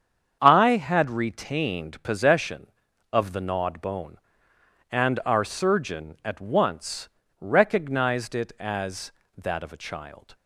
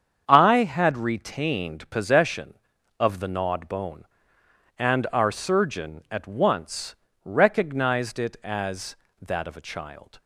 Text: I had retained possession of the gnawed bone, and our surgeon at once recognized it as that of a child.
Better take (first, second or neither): neither